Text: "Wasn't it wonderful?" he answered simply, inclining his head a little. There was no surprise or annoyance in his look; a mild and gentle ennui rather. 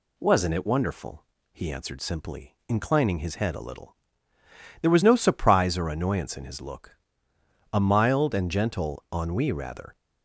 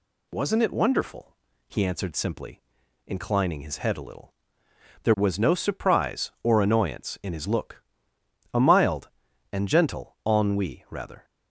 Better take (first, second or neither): neither